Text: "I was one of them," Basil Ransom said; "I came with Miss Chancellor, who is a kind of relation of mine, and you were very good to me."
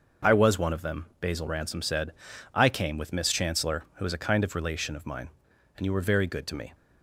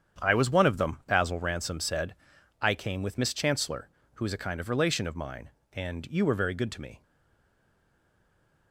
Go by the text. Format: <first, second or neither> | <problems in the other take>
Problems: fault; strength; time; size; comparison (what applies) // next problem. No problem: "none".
first | starts louder than the rest; strong; until 1.2 s; 8.5 dB; also in the first // stays silent after the last word; noticeable; from 7.0 s on; 1.7 s long